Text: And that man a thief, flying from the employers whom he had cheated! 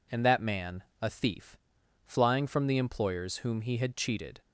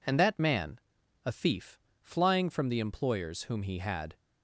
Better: first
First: pauses between "man" and "a"; slight; at 0.8 s; 0.18 s long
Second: pauses between "man" and "a"; noticeable; at 0.7 s; 0.46 s long // stops before "cheated"; at 4.1 s

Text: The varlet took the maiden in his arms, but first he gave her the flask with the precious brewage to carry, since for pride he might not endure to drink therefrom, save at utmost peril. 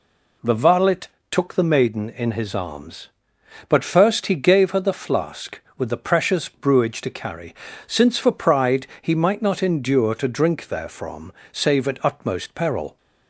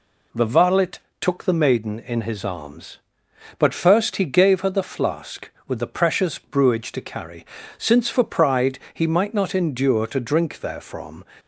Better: first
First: pauses between "varlet" and "took"; slight; at 1.0 s; 0.22 s long // pauses between "pride" and "he"; slight; at 8.8 s; 0.16 s long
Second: pauses between "varlet" and "took"; slight; at 1.0 s; 0.20 s long // pauses between "pride" and "he"; slight; at 8.7 s; 0.16 s long // stops before "save at utmost peril"; at 11.3 s

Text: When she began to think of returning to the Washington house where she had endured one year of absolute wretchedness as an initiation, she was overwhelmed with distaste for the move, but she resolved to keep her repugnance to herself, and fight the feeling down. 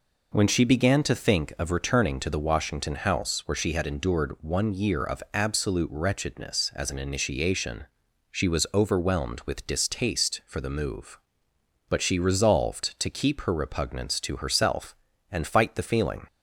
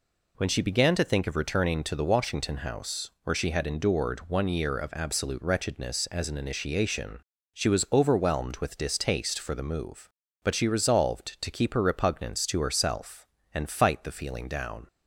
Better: second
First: stops before "down"; at 16.2 s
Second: none

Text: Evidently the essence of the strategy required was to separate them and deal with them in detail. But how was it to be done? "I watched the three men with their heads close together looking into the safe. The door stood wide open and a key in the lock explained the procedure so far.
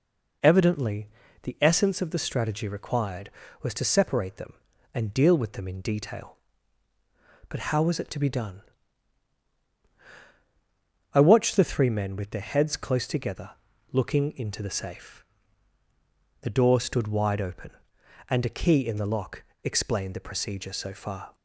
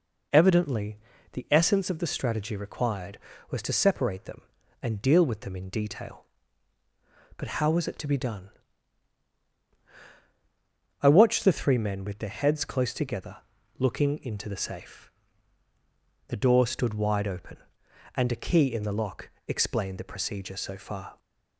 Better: neither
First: pauses between "Evidently" and "the"; slight; at 1.0 s; 0.36 s long // pauses between "together" and "looking"; at 13.5 s; 0.40 s long // pauses between "lock" and "explained"; slight; at 19.4 s; 0.20 s long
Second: pauses between "Evidently" and "the"; slight; at 0.9 s; 0.36 s long // pauses between "together" and "looking"; at 13.3 s; 0.40 s long // pauses between "lock" and "explained"; slight; at 19.2 s; 0.18 s long

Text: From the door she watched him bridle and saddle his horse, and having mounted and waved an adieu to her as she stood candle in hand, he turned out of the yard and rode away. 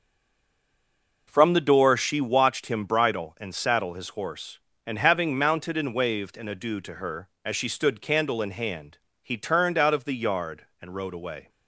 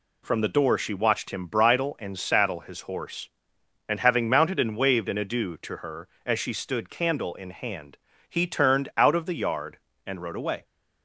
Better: second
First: stays silent before the first word; noticeable; until 1.2 s; 1.2 s long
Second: none

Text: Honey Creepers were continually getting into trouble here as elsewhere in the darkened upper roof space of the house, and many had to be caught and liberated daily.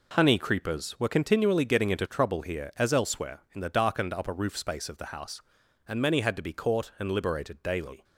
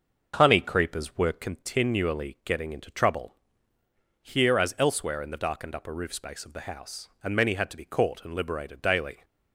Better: first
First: none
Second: starts louder than the rest; noticeable; until 1.5 s; 6 dB // pauses between "trouble" and "here"; noticeable; at 3.3 s; 0.84 s long

